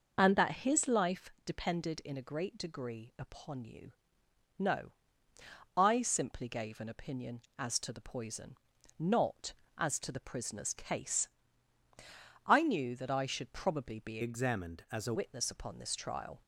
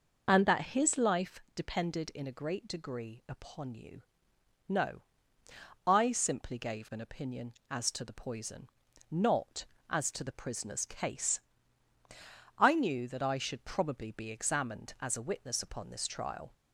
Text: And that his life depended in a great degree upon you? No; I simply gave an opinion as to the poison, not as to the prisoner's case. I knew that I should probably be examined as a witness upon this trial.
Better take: second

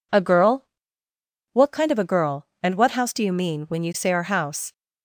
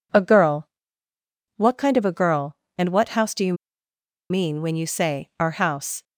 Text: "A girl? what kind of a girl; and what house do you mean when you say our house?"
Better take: first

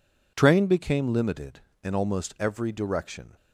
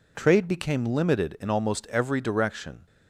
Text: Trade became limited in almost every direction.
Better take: second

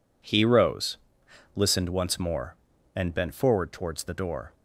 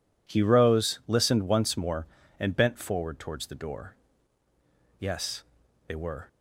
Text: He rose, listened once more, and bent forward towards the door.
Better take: first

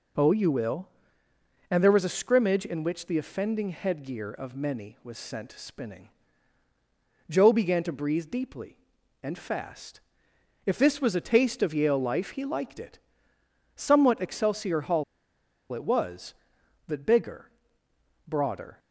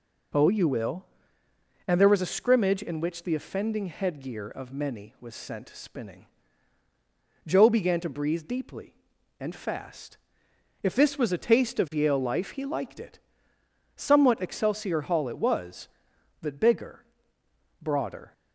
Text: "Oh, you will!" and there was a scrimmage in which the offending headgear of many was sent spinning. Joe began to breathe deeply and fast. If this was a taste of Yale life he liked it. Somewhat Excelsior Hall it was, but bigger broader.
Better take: second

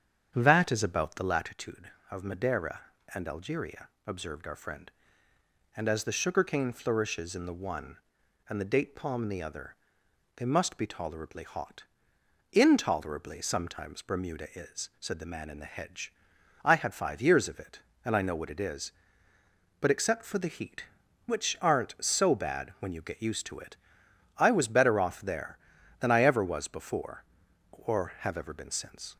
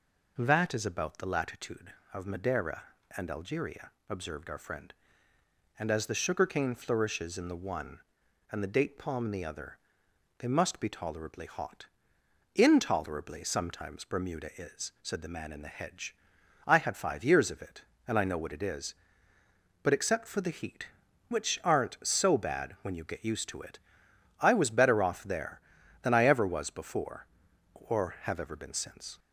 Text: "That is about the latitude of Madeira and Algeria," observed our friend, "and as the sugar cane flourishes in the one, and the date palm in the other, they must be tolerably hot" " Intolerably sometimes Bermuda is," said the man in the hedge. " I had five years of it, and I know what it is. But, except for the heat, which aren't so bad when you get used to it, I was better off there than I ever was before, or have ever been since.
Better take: second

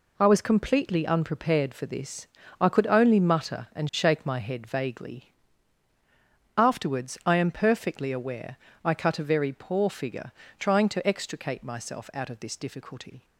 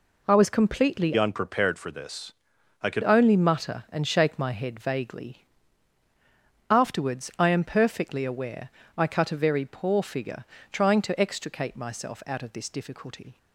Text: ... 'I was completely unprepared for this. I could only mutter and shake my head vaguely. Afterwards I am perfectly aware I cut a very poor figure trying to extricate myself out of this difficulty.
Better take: first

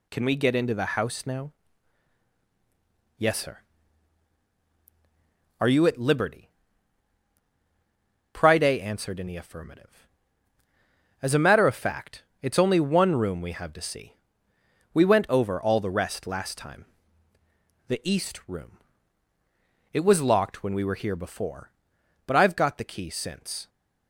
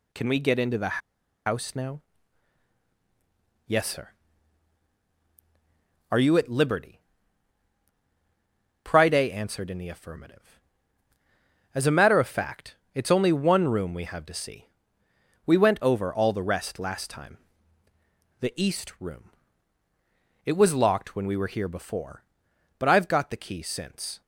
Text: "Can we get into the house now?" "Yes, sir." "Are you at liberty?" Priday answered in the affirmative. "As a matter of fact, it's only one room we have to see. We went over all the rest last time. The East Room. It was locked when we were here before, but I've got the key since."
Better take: first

